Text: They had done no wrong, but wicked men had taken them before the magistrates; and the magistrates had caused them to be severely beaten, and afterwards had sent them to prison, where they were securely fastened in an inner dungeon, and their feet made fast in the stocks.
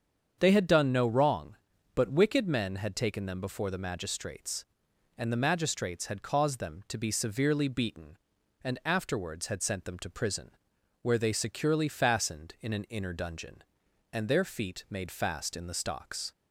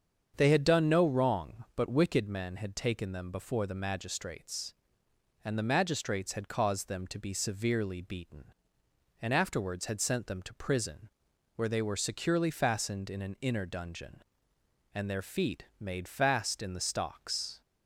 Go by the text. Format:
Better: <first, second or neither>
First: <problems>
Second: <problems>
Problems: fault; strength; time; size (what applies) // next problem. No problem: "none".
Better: second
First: starts louder than the rest; strong; until 1.4 s; 7.5 dB // skips "were"; at 11.3 s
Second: starts louder than the rest; strong; until 1.3 s; 7.5 dB